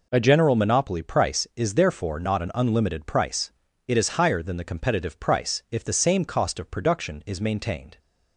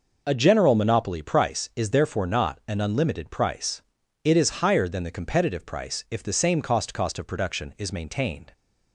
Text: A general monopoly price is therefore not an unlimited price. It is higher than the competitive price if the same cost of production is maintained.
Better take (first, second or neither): first